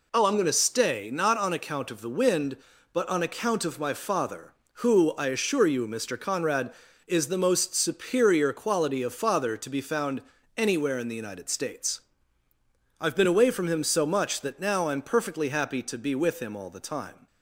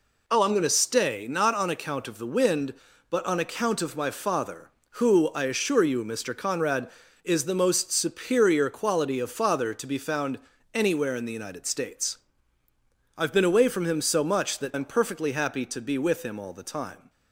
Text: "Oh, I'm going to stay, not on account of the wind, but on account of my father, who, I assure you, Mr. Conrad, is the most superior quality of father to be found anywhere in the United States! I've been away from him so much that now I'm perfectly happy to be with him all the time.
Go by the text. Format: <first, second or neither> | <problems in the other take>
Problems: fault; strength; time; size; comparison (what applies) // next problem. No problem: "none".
first | pauses between "found" and "anywhere"; slight; at 10.3 s; 0.36 s long; slight in the first // skips "now"; at 14.7 s